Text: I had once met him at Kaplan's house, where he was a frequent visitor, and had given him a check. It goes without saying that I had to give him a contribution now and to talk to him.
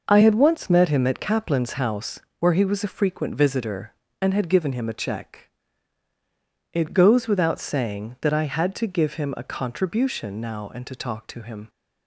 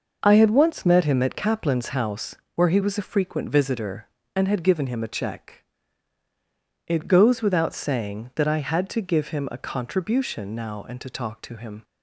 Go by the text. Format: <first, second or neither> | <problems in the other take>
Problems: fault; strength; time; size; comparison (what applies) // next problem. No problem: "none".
neither | none